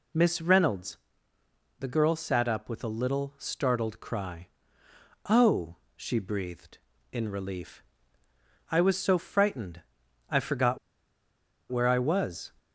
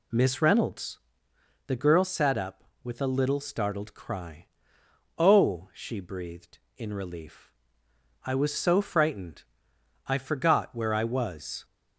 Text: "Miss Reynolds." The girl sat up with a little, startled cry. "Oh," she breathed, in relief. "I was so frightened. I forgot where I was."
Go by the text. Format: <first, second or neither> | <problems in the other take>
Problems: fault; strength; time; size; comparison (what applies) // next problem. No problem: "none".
second | pauses between "forgot" and "where"; noticeable; at 10.7 s; 0.93 s long